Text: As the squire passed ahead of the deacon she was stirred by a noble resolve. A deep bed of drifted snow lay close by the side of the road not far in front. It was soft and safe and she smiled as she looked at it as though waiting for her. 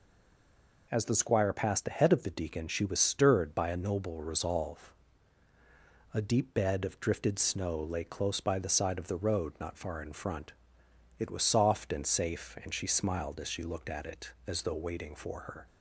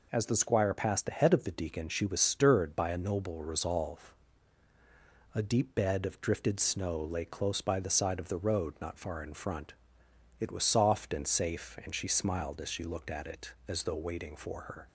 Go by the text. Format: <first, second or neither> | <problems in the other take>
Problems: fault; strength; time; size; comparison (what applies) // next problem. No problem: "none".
second | stays silent before the first word; slight; until 0.9 s; 0.9 s long